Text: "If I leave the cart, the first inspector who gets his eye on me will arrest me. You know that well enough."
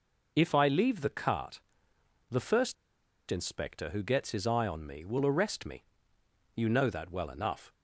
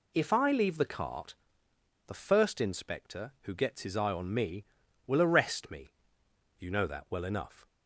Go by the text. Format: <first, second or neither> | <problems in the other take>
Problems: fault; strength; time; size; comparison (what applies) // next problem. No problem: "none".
second | pauses between "first" and "inspector"; noticeable; at 2.7 s; 0.55 s long